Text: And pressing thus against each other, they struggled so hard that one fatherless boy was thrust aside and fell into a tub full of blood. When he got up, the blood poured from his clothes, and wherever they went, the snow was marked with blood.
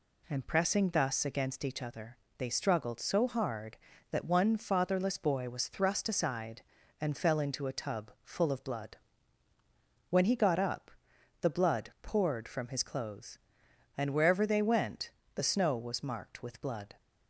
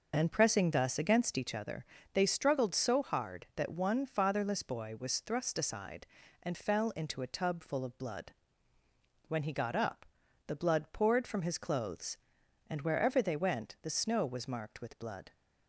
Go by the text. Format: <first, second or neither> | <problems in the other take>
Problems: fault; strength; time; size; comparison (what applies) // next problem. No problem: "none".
neither | none